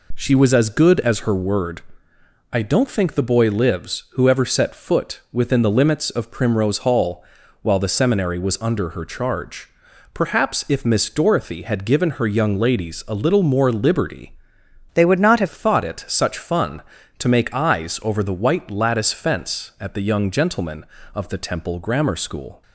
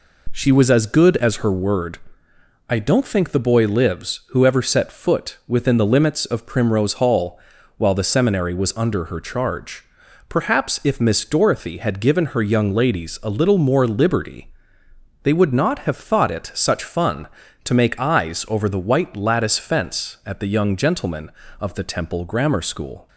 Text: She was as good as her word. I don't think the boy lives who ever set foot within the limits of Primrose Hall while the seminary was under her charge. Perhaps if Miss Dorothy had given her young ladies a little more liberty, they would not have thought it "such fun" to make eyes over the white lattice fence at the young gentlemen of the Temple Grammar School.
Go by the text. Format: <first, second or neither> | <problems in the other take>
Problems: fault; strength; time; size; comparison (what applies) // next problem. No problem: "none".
second | pauses between "Hall" and "while"; at 7.2 s; 0.38 s long; also in the second // changes voice from "they" to "have"; from 14.9 to 15.4 s; 0.5 s long